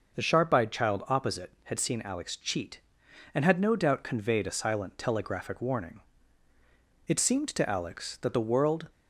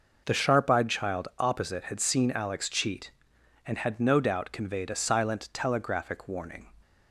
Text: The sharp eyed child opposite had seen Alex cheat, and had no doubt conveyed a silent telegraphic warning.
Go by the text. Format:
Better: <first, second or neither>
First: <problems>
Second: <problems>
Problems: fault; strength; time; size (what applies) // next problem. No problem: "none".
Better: second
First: goes on to say "It seemed to Alex that the world"; strong; from 7.0 s on; 1.8 s long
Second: none